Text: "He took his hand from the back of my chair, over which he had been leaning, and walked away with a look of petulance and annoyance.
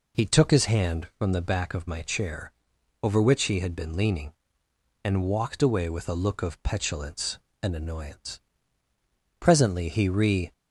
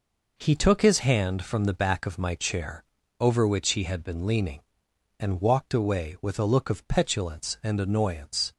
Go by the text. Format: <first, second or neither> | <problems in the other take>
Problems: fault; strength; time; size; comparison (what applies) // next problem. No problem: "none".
second | goes on to say "Presently he re"; noticeable; from 9.3 s on; 1.1 s long